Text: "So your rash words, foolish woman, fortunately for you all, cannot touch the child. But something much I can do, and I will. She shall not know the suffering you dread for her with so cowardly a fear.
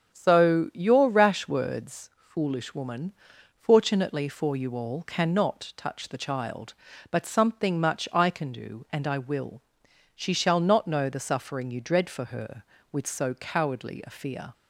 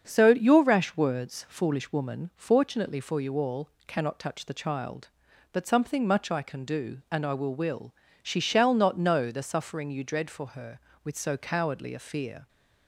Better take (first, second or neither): first